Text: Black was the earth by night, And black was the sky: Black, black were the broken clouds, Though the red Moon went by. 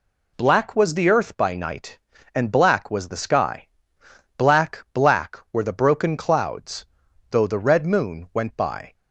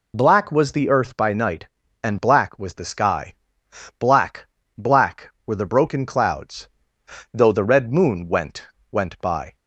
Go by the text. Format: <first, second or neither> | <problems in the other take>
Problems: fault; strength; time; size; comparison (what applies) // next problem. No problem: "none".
first | says "went" twice; at 8.9 s